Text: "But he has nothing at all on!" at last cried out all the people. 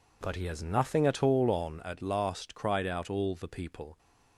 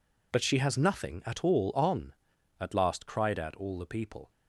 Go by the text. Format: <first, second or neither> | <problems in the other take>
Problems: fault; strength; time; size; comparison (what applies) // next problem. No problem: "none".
first | says "she" for "he"; at 0.4 s